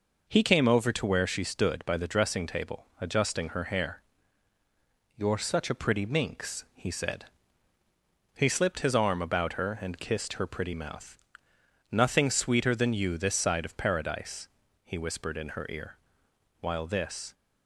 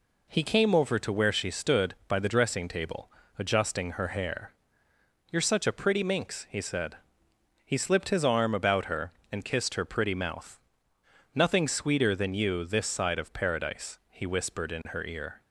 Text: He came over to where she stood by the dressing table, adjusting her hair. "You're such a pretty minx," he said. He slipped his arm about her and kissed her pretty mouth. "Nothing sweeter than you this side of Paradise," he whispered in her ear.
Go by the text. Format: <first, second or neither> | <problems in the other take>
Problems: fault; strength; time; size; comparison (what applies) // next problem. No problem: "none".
second | goes on to say "While this"; noticeable; from 16.5 s on; 0.74 s long